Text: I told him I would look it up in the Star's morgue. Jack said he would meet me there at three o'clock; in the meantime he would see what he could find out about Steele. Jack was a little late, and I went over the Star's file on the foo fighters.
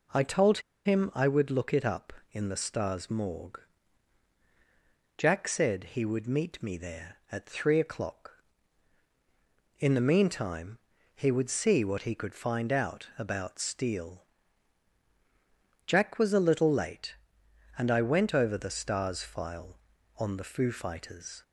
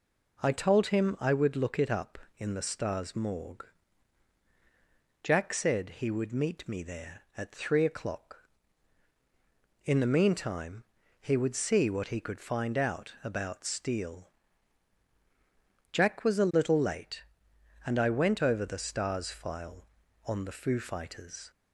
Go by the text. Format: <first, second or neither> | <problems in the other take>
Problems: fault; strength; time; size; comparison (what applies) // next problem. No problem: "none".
second | pauses between "told" and "him"; slight; at 0.5 s; 0.26 s long // pauses between "meantime" and "he"; slight; at 10.7 s; 0.36 s long; slight in the second